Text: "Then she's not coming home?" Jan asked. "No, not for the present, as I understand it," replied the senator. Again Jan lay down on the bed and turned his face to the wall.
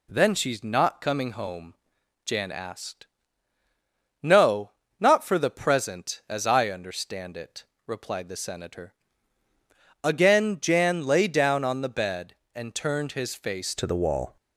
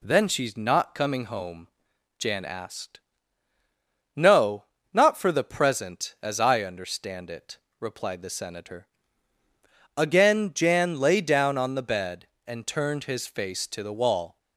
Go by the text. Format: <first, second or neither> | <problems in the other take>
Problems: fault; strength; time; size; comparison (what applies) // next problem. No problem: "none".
second | changes voice at "to"; from 13.7 s on; 0.6 s long